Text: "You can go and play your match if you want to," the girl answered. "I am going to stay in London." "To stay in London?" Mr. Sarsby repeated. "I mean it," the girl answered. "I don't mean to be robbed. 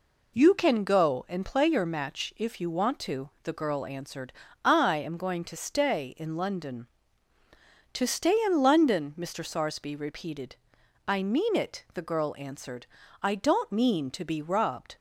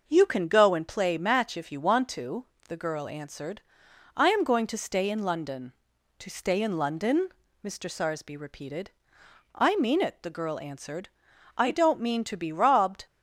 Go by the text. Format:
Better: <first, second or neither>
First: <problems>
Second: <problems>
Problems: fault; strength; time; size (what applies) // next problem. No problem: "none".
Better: first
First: none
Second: starts louder than the rest; noticeable; until 1.0 s; 6 dB // skips "your"; at 1.1 s